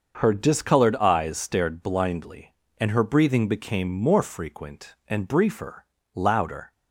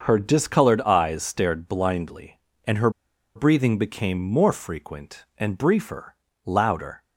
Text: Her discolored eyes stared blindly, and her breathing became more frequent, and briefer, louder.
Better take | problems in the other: first | starts louder than the rest; until 1.0 s; 6.5 dB; also in the first // pauses between "her" and "breathing"; noticeable; at 2.8 s; 0.46 s long

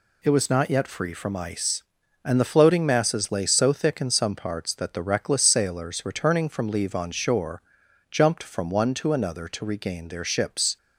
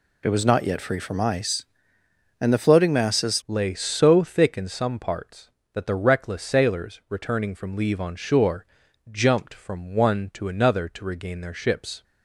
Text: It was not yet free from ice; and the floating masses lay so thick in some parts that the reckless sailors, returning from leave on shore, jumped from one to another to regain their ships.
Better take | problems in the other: first | changes voice at "lay"; from 3.4 s on; 8.6 s long

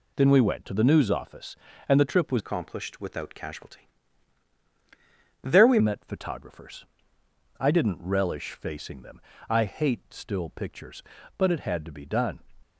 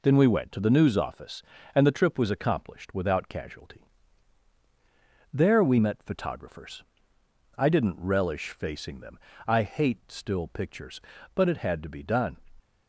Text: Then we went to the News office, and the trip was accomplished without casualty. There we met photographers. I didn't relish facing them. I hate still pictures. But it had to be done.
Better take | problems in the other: second | changes voice from "accomplished" to "we"; from 2.3 to 5.7 s; 3.4 s long

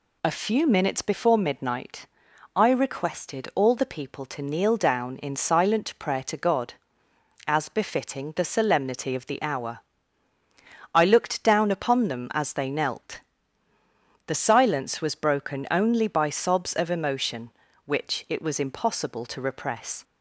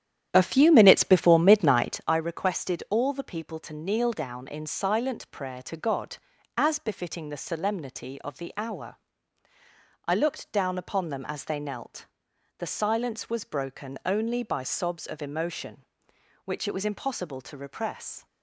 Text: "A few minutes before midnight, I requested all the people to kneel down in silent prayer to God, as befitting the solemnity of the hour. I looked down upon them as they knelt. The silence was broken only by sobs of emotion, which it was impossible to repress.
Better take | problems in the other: first | starts louder than the rest; strong; until 2.2 s; 10.5 dB

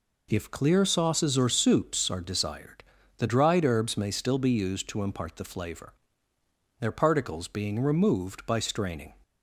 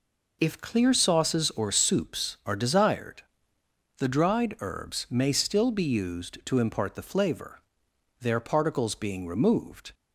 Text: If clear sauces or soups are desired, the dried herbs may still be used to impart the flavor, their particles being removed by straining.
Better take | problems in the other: first | stops before "by straining"; at 9.9 s

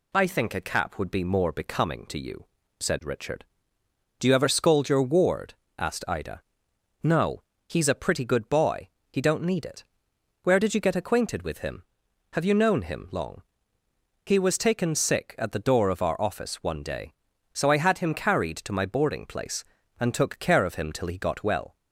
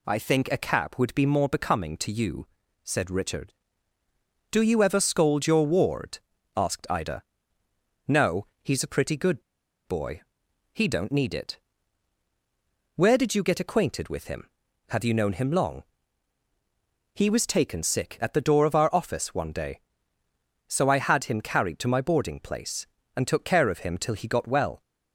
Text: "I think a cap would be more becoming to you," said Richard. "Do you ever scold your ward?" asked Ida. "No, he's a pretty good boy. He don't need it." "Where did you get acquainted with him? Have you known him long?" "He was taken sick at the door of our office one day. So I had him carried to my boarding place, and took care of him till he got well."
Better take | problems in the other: first | pauses between "good" and "boy"; at 9.4 s; 0.44 s long

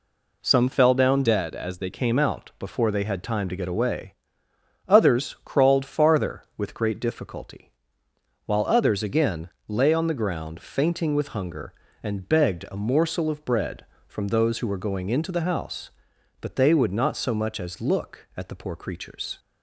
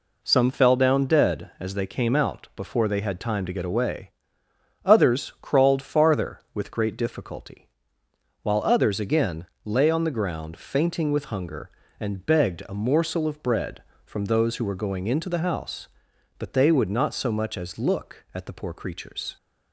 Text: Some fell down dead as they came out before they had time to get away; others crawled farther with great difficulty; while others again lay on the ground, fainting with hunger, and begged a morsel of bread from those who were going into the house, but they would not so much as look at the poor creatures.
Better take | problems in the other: second | changes voice from "dead" to "they"; from 1.2 to 1.8 s; 0.6 s long // pauses between "again" and "lay"; slight; at 9.4 s; 0.18 s long; slight in the second

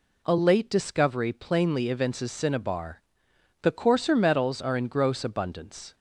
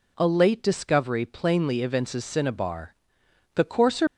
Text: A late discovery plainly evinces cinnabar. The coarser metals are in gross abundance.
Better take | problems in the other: first | stops before "metals are in gross abundance"; at 4.0 s

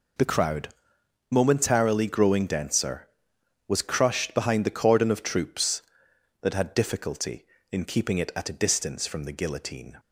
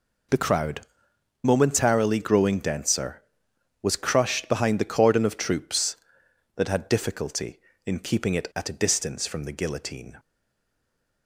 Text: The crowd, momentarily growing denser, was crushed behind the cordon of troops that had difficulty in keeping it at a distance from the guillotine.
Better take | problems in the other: first | stays silent after the last word; from 10.1 s on; 1.1 s long

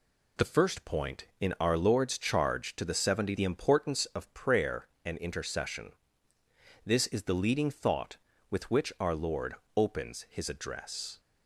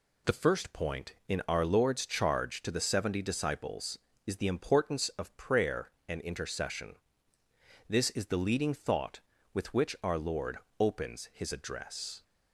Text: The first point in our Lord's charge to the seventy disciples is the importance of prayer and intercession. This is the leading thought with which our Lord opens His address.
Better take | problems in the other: second | skips "disciples is"; at 3.3 s // pauses between "Lord" and "opens"; slight; at 9.5 s; 0.20 s long; slight in the second

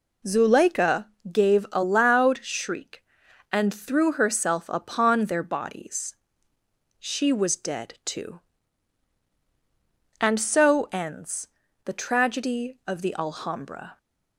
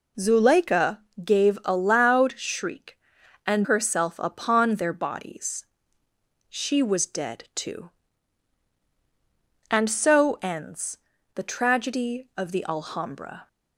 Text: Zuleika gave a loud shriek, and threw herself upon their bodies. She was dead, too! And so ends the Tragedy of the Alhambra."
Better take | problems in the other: first | pauses between "Zuleika" and "gave"; slight; at 0.9 s; 0.24 s long; slight in the first // skips "threw"; at 3.6 s // pauses between "ends" and "the"; at 10.9 s; 0.38 s long; also in the first

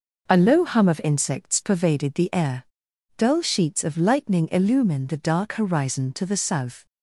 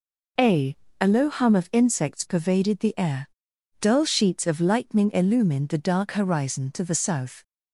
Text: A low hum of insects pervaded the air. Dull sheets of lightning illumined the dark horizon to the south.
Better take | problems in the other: first | says "A" twice; at 1.0 s

